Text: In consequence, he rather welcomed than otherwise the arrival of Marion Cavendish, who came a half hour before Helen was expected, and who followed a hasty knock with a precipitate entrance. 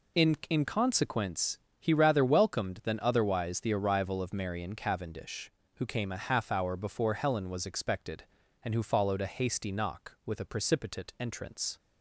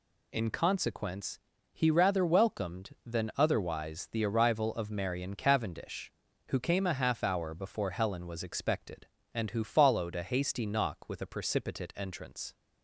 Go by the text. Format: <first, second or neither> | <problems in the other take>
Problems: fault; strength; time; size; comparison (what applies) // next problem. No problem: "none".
second | says "In" twice; at 0.4 s